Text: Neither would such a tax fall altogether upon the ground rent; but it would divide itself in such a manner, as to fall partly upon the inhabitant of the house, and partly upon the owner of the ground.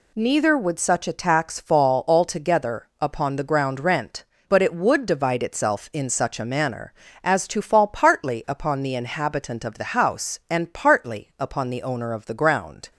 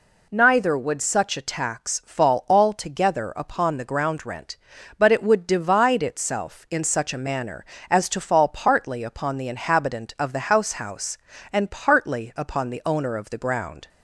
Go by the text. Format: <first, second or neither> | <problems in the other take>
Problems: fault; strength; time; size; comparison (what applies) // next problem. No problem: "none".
first | says "house" twice; at 10.7 s